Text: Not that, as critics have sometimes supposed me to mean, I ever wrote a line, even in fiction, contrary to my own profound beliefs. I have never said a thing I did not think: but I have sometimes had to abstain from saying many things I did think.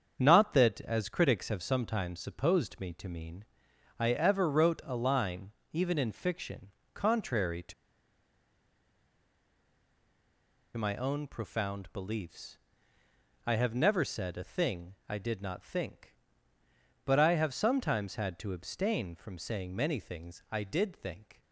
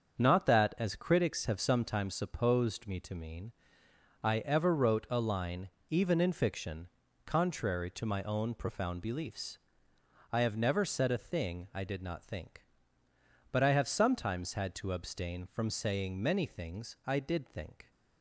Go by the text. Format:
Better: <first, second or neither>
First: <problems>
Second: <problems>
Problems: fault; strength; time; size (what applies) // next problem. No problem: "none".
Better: second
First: starts louder than the rest; until 1.1 s; 7 dB // pauses between "to" and "my"; strong; at 7.7 s; 3.0 s long // pauses between "thing" and "I"; slight; at 14.9 s; 0.16 s long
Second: starts louder than the rest; until 1.2 s; 7 dB